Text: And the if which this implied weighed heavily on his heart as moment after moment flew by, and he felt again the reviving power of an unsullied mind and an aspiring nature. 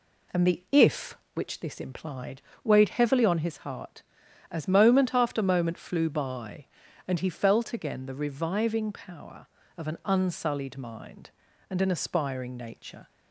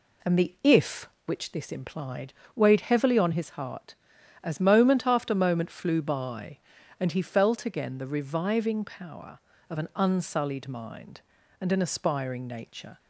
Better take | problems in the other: neither | pauses between "implied" and "weighed"; slight; the same in both

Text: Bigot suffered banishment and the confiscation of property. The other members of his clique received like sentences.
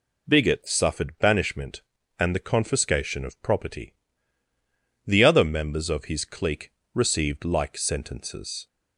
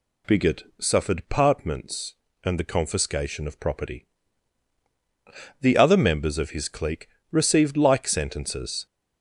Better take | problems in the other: first | pauses between "Bigot" and "suffered"; slight; at 0.6 s; 0.16 s long // says "partments" for "banishment"; at 1.2 s // pauses between "clique" and "received"; slight; at 7.0 s; 0.24 s long; slight in the first

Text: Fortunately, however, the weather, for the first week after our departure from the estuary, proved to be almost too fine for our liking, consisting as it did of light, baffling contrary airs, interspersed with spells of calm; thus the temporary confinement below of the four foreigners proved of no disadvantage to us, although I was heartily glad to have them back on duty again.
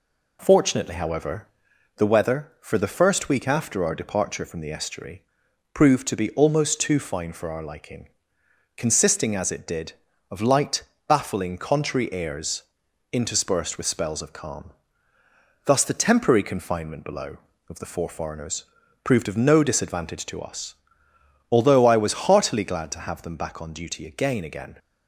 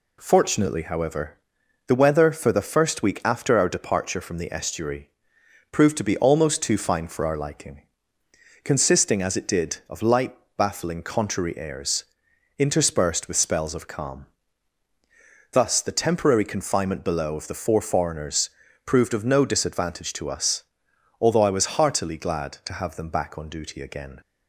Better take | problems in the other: second | pauses between "foreigners" and "proved"; at 18.6 s; 0.40 s long; slight in the second // says "again" twice; at 24.4 s

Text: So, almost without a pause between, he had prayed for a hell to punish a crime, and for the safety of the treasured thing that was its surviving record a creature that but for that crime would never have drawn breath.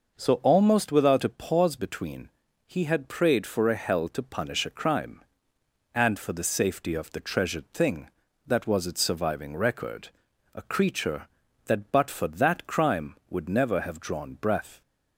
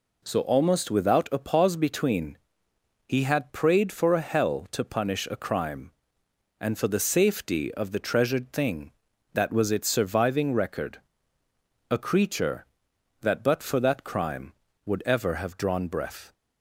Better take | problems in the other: first | pauses between "record" and "a"; noticeable; at 10.9 s; 0.90 s long; also in the first // says "ever" for "never"; at 15.0 s

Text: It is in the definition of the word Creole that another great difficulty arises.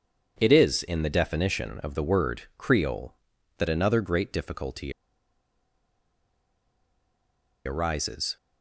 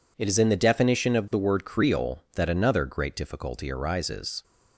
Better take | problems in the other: second | pauses between "difficulty" and "arises"; strong; at 4.9 s; 2.7 s long

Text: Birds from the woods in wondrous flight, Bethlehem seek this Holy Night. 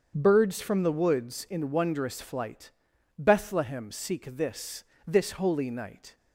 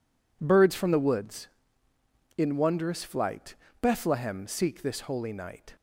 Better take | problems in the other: second | starts louder than the rest; until 1.1 s; 7 dB // says "this" twice; at 5.0 s

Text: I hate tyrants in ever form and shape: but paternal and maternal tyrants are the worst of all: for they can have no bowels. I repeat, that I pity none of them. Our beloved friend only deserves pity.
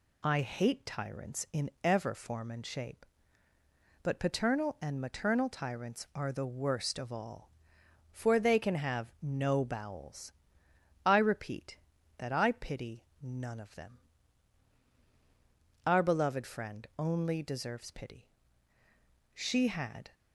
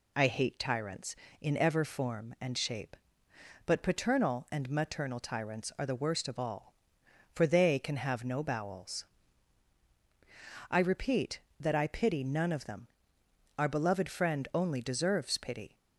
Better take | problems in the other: second | pauses between "pity" and "none"; slight; at 13.0 s; 0.18 s long // goes on to say "She had"; noticeable; from 19.3 s on; 0.78 s long

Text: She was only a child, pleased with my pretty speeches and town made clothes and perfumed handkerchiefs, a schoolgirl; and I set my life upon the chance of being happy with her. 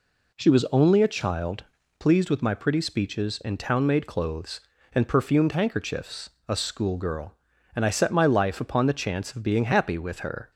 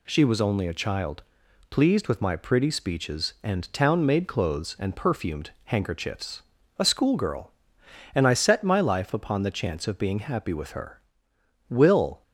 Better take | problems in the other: first | goes on to say "Will"; from 11.6 s on; 0.54 s long

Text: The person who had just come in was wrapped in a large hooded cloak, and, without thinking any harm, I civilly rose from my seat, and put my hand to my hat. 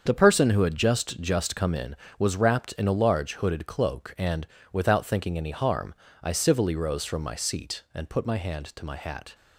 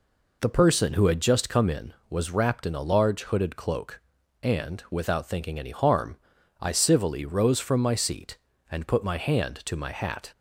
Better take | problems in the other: second | starts louder than the rest; until 1.0 s; 7 dB // says "just" twice; at 1.1 s

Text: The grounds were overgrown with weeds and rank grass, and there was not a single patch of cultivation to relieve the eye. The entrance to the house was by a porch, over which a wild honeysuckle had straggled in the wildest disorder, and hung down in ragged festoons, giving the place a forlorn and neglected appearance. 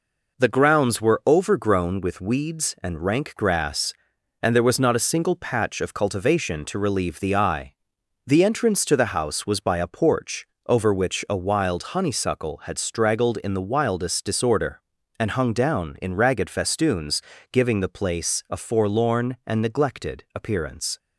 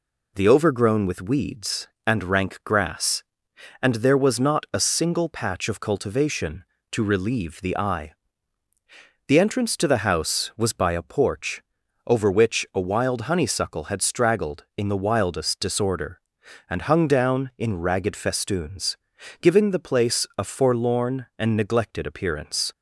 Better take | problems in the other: first | skips "grounds were"; at 0.4 s

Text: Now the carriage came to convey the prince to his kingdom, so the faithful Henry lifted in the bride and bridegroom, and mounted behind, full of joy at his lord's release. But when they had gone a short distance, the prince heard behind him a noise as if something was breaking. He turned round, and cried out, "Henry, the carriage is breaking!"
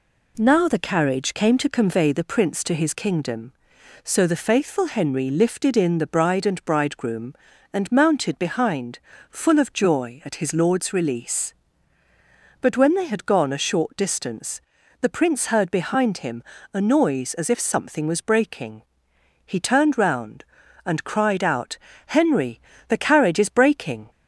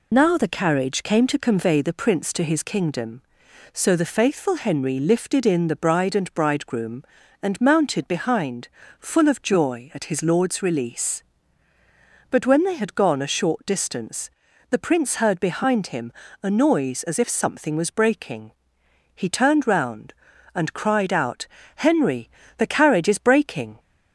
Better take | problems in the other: first | loses the start of "Now"; at 0.1 s; 75 ms // pauses between "him" and "a"; slight; at 16.1 s; 0.32 s long; slight in the first

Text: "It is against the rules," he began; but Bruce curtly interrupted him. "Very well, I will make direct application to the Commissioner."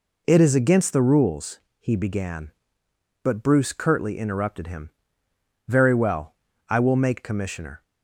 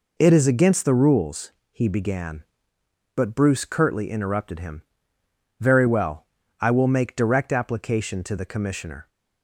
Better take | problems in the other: second | skips "direct application to the"; at 7.2 s

